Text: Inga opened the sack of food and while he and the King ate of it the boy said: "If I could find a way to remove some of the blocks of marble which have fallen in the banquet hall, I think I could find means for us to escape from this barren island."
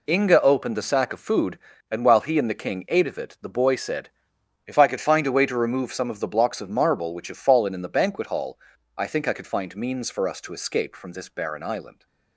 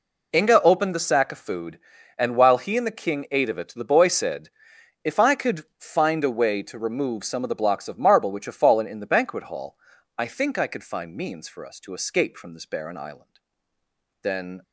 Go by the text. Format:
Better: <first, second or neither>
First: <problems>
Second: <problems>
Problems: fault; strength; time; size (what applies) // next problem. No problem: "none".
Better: first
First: none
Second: goes on to say "Then"; slight; from 14.2 s on; 0.40 s long